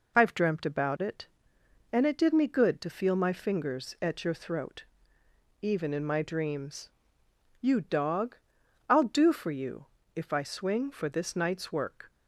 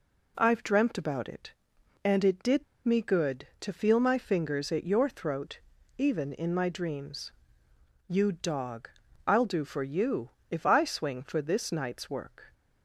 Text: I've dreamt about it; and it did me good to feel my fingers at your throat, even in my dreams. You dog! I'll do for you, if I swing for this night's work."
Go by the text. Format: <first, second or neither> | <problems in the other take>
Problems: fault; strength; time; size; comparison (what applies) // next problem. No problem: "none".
first | pauses between "did" and "me"; slight; at 2.6 s; 0.22 s long